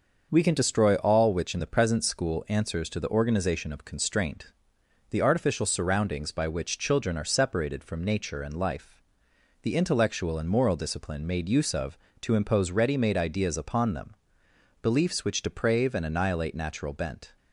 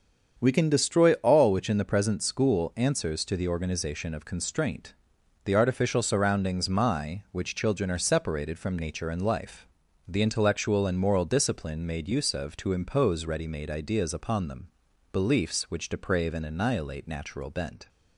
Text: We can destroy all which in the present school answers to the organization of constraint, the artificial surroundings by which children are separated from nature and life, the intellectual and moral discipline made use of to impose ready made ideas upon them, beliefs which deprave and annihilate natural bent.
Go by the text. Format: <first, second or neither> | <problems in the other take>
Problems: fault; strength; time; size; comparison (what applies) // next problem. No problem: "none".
first | starts louder than the rest; until 1.4 s; 7 dB; noticeable in the first // says "my" for "by"; at 6.6 s